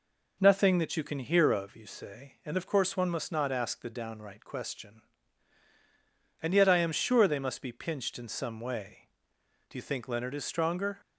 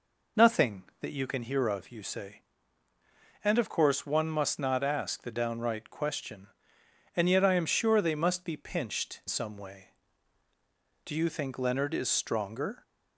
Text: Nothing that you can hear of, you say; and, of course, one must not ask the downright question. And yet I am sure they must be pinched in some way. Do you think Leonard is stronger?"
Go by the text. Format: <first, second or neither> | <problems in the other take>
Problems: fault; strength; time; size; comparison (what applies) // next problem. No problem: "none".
first | skips "in"; at 9.2 s